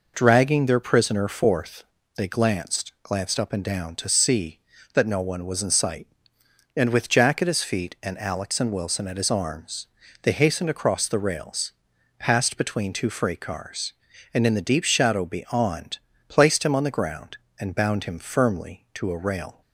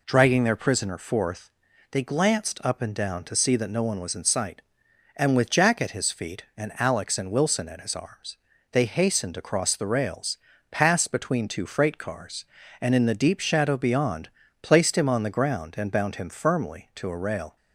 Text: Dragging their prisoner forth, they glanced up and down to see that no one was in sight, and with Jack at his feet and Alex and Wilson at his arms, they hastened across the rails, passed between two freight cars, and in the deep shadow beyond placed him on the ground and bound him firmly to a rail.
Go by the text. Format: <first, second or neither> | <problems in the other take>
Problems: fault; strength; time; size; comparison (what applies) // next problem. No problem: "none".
second | says "glanced" twice; at 3.0 s // pauses between "beyond" and "placed"; slight; at 15.9 s; 0.30 s long; slight in the second